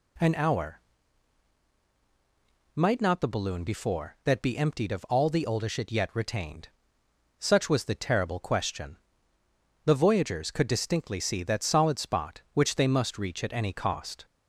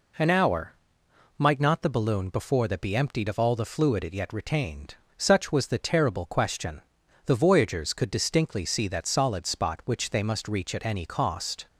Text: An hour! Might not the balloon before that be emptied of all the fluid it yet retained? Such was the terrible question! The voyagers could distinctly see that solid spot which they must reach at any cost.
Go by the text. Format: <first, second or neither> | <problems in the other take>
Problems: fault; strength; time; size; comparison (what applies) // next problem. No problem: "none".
second | says "oldish" for "fluid"; at 5.4 s